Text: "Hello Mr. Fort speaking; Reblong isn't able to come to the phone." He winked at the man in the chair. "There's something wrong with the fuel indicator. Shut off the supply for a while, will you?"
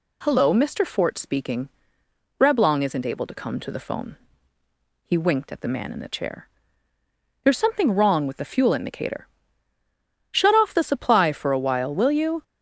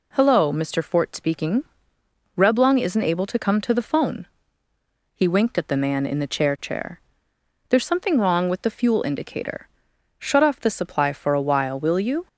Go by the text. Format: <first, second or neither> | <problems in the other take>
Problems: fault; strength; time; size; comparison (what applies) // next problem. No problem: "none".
first | says "chair" twice; at 6.5 s